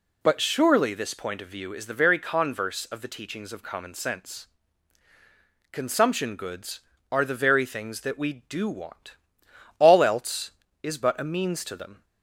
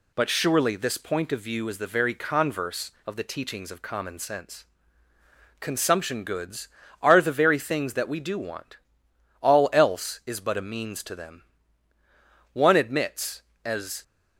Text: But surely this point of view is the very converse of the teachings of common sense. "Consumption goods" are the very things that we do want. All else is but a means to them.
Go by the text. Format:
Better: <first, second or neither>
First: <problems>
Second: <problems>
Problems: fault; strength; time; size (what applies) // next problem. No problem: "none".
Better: first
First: none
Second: goes on to say "One admits as"; from 12.5 s on; 1.5 s long